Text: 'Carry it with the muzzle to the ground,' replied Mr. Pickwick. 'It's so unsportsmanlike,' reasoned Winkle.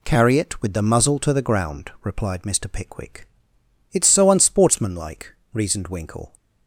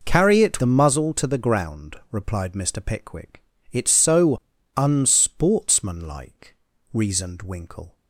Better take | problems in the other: first | skips "with"; at 0.5 s // pauses between "so" and "unsportsmanlike"; at 4.3 s; 0.38 s long

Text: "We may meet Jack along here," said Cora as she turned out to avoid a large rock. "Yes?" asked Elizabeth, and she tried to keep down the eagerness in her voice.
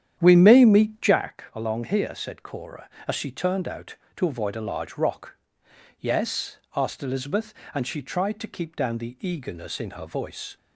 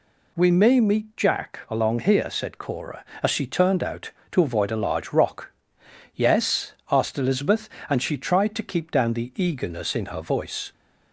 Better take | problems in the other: second | starts louder than the rest; strong; until 1.3 s; 9.5 dB

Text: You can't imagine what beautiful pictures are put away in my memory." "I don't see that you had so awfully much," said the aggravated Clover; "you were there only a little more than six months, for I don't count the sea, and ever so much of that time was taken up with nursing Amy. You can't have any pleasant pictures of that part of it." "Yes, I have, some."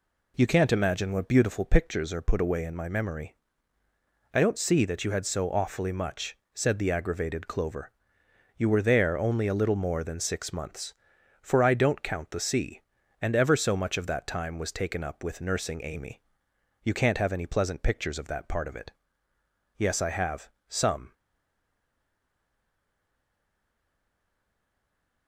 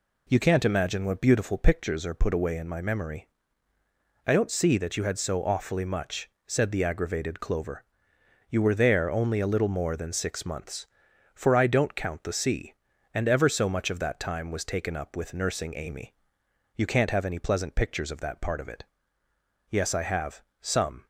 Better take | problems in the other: second | stays silent after the last word; strong; from 21.1 s on; 4.1 s long

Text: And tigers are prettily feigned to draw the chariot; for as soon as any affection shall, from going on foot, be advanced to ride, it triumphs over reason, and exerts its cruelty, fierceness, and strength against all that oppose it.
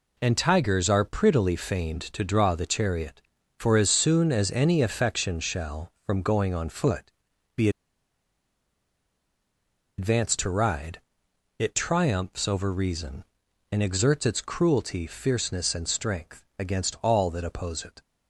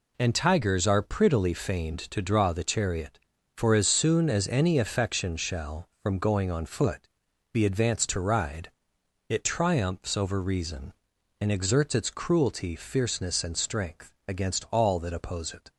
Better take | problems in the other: second | pauses between "be" and "advanced"; strong; at 7.6 s; 2.2 s long // pauses between "strength" and "against"; slight; at 16.4 s; 0.16 s long; slight in the second

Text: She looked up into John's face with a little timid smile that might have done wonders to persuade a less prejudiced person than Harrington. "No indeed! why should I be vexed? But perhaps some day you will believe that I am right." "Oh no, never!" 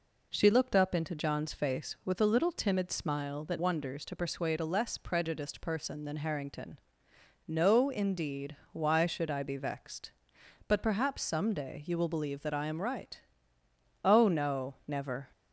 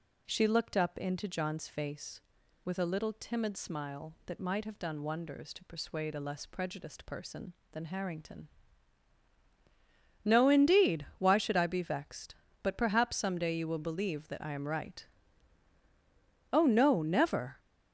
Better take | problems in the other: second | skips "might have done"; at 3.5 s

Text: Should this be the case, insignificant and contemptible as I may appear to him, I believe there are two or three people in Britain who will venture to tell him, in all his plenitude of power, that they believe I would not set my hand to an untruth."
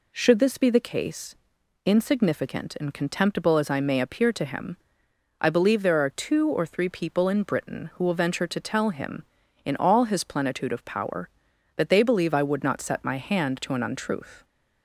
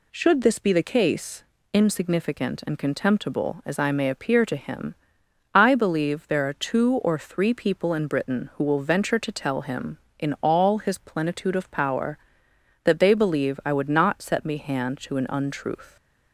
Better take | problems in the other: first | says "me" for "my"; at 14.4 s

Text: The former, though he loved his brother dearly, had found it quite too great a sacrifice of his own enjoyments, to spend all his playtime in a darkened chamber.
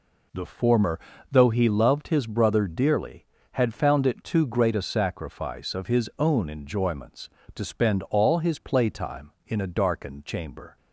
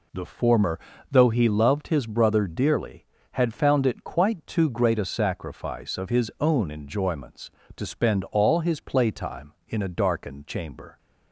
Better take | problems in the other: second | skips "quite"; at 4.2 s

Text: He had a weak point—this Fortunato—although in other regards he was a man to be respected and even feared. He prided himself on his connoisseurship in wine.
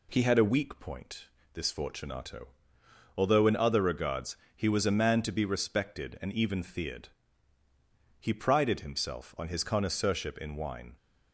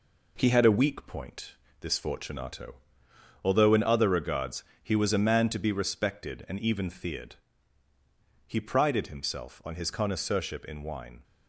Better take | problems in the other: first | gets quieter; noticeable; throughout; 5 dB // pauses between "regards" and "he"; slight; at 4.6 s; 0.20 s long; slight in the first

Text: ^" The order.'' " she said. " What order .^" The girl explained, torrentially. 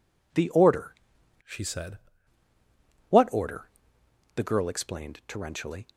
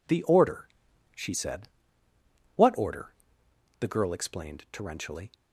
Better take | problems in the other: second | changes voice from "she" to "said"; from 1.4 to 1.9 s; 0.5 s long

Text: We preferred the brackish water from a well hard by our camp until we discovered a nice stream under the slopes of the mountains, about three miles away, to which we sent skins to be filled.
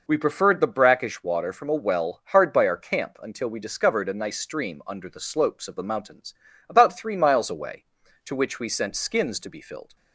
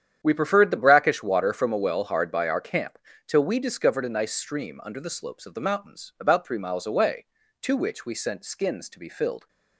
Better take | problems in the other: first | starts louder than the rest; strong; until 1.2 s; 9.5 dB // says "till" for "until"; at 3.2 s

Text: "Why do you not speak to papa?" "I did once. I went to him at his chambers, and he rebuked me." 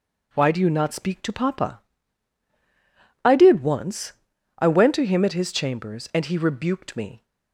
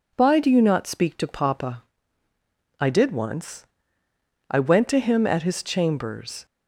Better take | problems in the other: first | stops before "and he rebuked me"; at 6.4 s

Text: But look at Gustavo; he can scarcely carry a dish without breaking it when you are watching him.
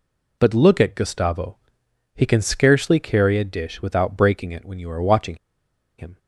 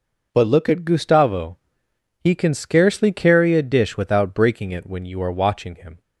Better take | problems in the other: second | pauses between "watching" and "him"; noticeable; at 5.3 s; 0.62 s long

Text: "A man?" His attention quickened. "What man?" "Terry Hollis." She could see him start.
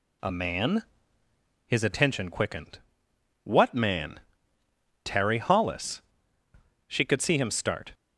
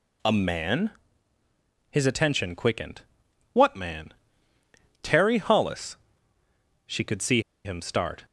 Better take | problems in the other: first | pauses between "see" and "him"; slight; at 7.3 s; 0.25 s long

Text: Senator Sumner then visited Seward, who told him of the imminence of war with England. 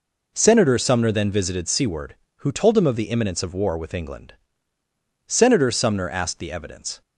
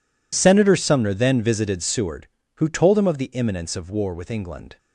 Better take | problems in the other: second | goes on to say "Senator Sumner asked the evidence"; strong; from 5.2 s on; 1.7 s long

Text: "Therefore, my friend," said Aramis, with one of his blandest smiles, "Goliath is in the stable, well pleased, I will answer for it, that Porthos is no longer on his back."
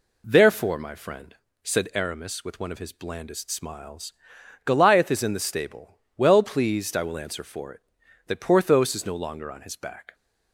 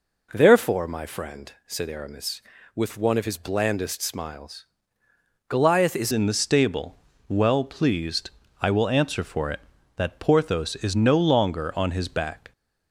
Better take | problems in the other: first | changes voice at "in"; from 6.1 s on; 6.4 s long

